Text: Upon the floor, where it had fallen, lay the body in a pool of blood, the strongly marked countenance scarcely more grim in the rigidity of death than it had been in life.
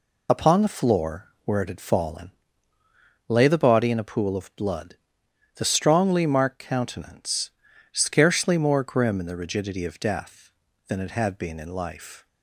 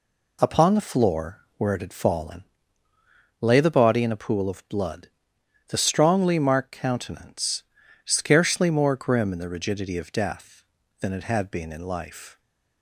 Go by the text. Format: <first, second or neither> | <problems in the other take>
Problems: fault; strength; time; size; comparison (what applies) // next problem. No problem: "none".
second | loses the start of "Upon"; at 0.2 s; 35 ms // pauses between "countenance" and "scarcely"; at 7.5 s; 0.42 s long; also in the second